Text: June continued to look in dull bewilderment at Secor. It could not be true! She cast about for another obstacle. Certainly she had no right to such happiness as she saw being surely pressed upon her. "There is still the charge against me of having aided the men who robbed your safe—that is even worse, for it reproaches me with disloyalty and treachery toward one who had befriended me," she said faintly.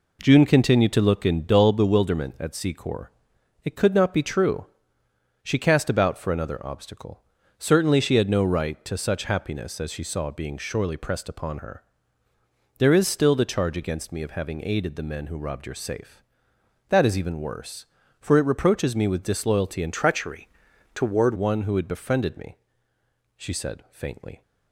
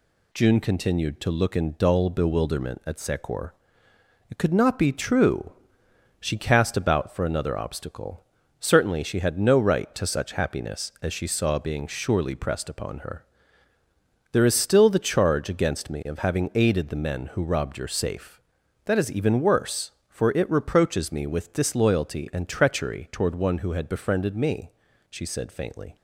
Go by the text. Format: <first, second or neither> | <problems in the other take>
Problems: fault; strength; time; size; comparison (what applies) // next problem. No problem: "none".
second | changes voice from "treachery" to "toward"; from 19.9 to 21.3 s; 1.4 s long // pauses between "treachery" and "toward"; noticeable; at 20.4 s; 0.48 s long